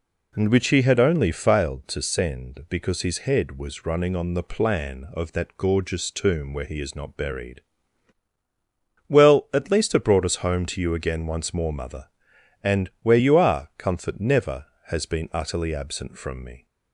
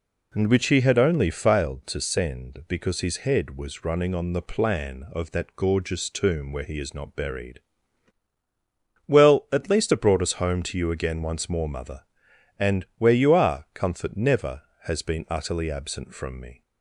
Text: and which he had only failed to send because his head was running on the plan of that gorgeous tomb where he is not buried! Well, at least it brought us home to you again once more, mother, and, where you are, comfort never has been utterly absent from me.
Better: neither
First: none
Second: none

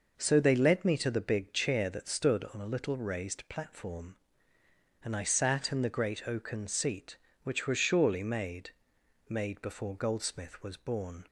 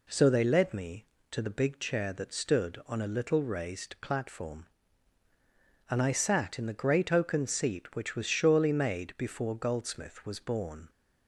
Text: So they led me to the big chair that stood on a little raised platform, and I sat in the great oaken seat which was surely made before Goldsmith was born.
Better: second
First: says "made" twice; at 9.2 s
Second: none

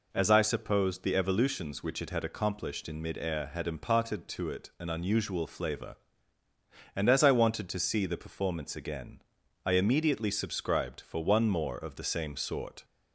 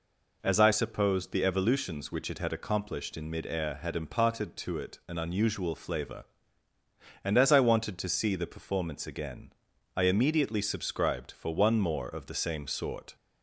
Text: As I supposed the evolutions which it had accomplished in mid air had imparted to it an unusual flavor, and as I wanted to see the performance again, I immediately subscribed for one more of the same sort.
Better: neither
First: none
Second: none

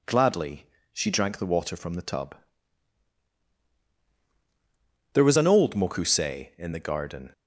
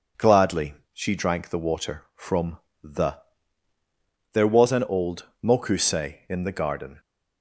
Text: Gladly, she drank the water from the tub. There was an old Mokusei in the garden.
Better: first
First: none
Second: pauses between "from" and "the"; slight; at 2.5 s; 0.24 s long // skips "tub"; at 3.7 s // pauses between "old" and "Mokusei"; slight; at 5.2 s; 0.20 s long

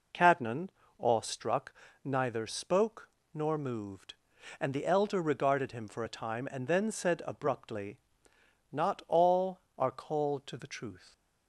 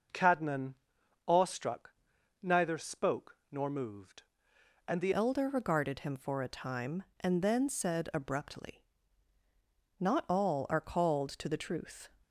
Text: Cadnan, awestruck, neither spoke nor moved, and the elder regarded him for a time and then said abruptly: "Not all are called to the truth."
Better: first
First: pauses between "spoke" and "nor"; slight; at 3.0 s; 0.24 s long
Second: pauses between "spoke" and "nor"; slight; at 3.3 s; 0.16 s long // changes voice at "elder"; from 5.1 s on; 6.9 s long

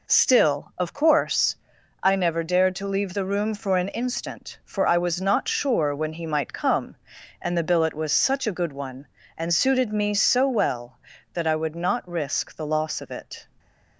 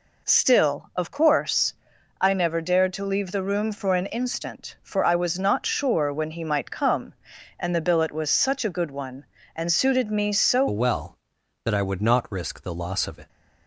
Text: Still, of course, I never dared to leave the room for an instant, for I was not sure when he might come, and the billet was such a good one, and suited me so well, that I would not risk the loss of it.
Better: first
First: none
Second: changes voice at "well"; from 10.6 s on; 2.6 s long

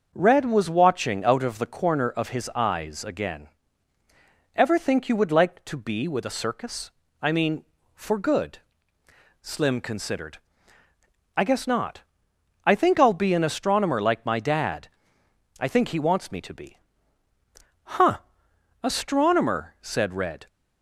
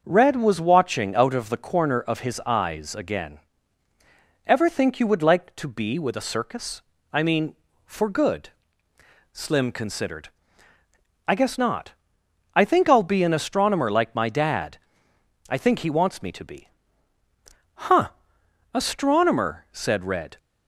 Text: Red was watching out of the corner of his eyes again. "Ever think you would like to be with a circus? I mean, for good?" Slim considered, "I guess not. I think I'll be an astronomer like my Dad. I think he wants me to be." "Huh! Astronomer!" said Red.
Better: neither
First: starts louder than the rest; until 1.1 s; 6 dB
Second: starts louder than the rest; until 1.0 s; 6 dB

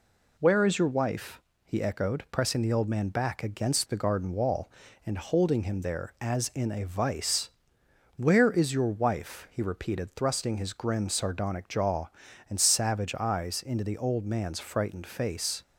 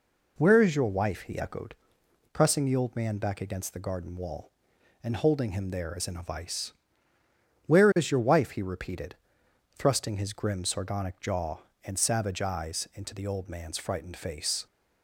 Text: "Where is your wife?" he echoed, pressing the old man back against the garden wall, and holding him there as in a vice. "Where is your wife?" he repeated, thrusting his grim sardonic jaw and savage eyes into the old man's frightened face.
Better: neither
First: none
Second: none

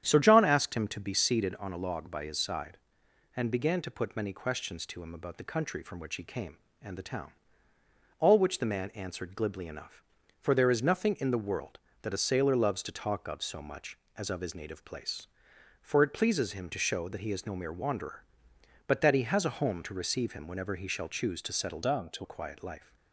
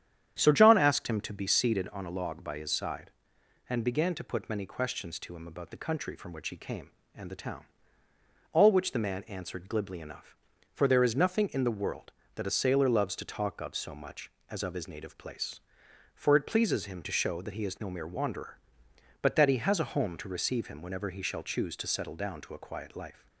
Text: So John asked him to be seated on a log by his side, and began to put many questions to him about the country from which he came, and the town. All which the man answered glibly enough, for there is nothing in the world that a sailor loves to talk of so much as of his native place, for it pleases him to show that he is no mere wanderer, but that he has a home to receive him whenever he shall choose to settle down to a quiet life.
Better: second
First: starts louder than the rest; strong; until 1.0 s; 9.5 dB // changes voice from "down" to "to"; from 21.8 to 22.2 s; 0.4 s long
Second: starts louder than the rest; strong; until 1.4 s; 9.5 dB

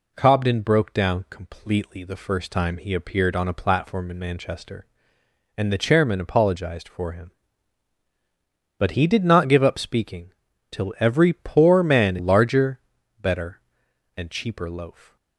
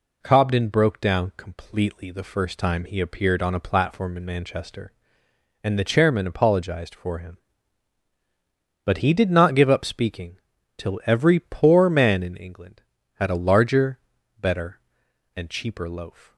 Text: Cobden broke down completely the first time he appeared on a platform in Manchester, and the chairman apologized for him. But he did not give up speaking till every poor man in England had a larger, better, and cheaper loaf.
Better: second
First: pauses between "speaking" and "till"; at 10.3 s; 0.40 s long // skips "in England had a"; at 12.1 s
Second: pauses between "speaking" and "till"; at 10.3 s; 0.40 s long

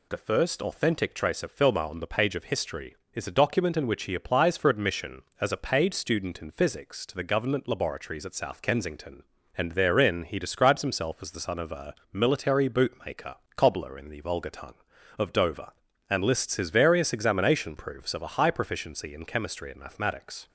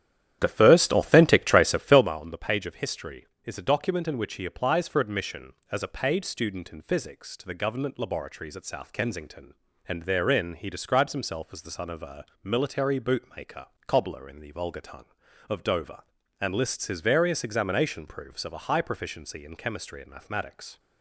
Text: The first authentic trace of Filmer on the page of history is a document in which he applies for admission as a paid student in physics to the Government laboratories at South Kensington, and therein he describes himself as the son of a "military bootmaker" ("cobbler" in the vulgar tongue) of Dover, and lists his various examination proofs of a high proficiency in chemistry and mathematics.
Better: first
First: pauses between "a" and "military"; slight; at 11.9 s; 0.16 s long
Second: starts louder than the rest; strong; until 2.1 s; 11 dB // pauses between "a" and "military"; slight; at 12.2 s; 0.16 s long

